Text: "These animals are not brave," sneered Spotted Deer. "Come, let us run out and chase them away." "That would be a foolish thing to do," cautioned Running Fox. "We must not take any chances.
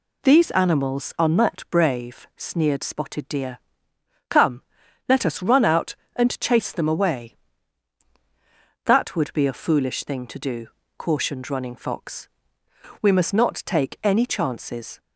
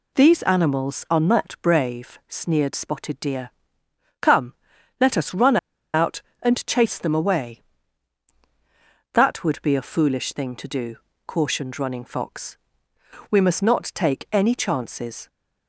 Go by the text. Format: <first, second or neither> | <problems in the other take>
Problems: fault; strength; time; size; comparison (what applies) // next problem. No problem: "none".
first | pauses between "run" and "out"; at 5.5 s; 0.37 s long